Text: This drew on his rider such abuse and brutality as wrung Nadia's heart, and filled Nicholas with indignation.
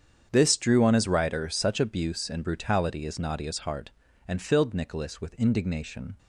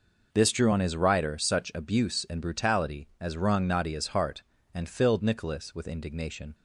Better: second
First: starts louder than the rest; strong; until 1.3 s; 8 dB // skips "wrung"; at 3.1 s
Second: none

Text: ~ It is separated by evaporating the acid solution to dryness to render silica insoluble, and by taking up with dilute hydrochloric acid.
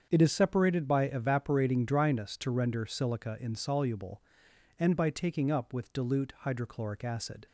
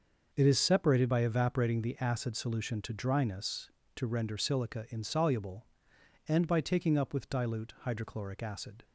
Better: second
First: starts louder than the rest; strong; until 1.1 s; 7.5 dB // skips "the acid solution to"; at 1.8 s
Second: starts louder than the rest; noticeable; until 1.3 s; 6 dB

